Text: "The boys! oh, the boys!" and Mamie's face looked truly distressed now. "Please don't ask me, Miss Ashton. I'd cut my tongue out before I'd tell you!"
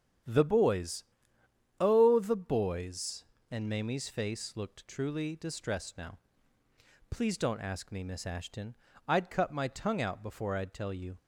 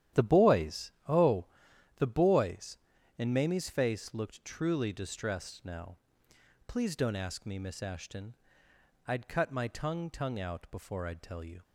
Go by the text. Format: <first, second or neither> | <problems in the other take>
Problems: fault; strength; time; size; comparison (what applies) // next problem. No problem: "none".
first | starts louder than the rest; strong; until 1.3 s; 11.5 dB; strong in the first // says "tongue" twice; at 10.1 s